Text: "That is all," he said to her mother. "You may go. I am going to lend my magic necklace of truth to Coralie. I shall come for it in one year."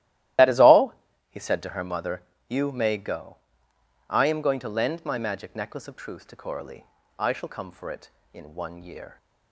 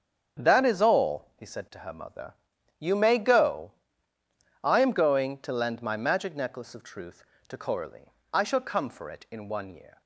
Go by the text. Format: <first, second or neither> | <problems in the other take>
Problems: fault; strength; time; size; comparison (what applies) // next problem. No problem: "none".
second | loses the start of "That"; at 0.3 s; 50 ms // starts louder than the rest; strong; until 1.7 s; 14.5 dB; strong in the second